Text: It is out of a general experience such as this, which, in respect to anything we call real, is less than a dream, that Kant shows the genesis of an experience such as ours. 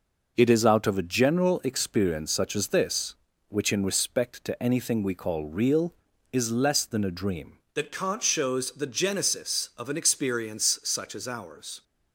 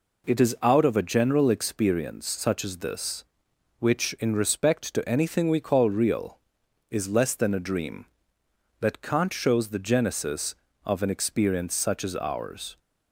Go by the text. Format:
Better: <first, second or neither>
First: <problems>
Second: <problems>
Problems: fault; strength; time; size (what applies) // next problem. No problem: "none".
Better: second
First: changes voice at "that"; from 7.7 s on; 4.1 s long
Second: none